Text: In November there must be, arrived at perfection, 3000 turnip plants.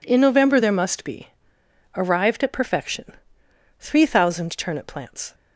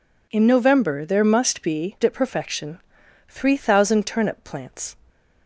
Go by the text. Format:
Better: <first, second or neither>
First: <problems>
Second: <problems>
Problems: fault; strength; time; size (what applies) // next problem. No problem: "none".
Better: first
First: none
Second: skips "arrived"; at 1.9 s